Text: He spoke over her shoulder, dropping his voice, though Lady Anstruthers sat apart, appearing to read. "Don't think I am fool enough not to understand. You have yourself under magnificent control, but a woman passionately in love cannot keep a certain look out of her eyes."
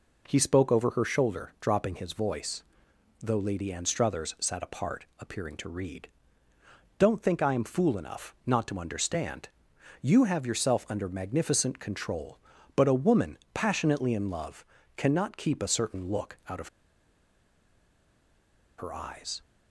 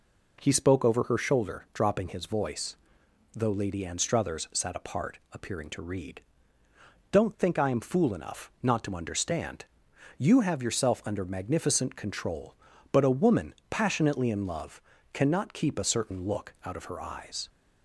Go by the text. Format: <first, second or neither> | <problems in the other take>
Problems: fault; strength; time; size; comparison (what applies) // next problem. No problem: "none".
second | pauses between "woman" and "passionately"; slight; at 13.3 s; 0.16 s long; slight in the second // pauses between "love" and "cannot"; slight; at 14.6 s; 0.32 s long; slight in the second // pauses between "of" and "her"; strong; at 16.6 s; 2.0 s long